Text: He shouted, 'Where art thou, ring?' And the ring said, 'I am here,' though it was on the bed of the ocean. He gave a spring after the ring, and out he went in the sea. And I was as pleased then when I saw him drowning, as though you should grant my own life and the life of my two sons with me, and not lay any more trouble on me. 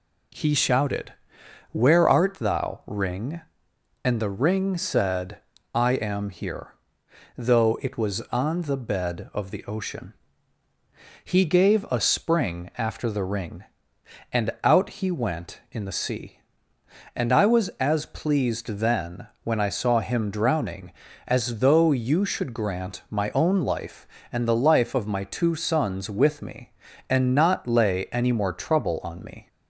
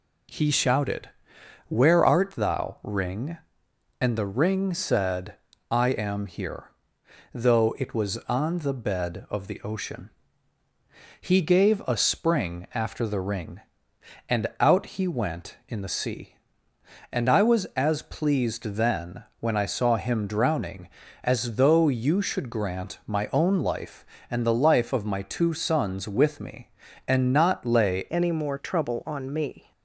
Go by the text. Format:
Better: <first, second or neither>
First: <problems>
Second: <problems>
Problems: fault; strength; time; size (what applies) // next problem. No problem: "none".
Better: first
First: pauses between "then" and "when"; slight; at 19.2 s; 0.16 s long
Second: pauses between "then" and "when"; slight; at 19.2 s; 0.16 s long // changes voice at "any"; from 28.1 s on; 1.6 s long